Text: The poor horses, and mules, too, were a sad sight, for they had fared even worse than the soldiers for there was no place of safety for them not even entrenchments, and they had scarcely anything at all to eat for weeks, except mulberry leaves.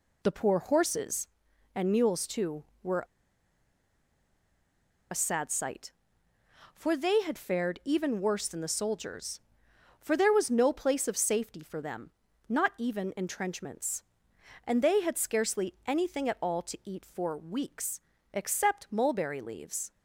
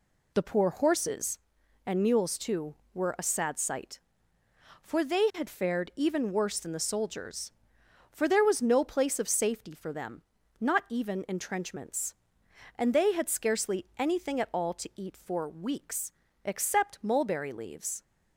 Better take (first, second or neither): second